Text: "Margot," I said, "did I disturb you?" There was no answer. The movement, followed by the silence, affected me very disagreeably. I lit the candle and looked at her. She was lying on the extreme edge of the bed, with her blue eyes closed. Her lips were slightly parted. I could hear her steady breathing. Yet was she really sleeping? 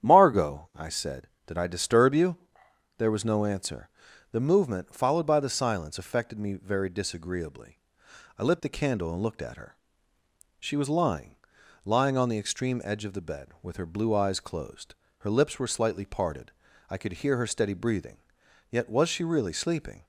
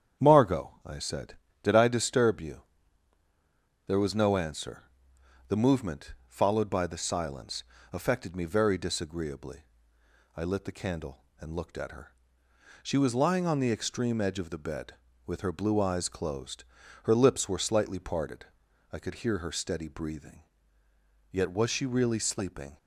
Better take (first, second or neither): second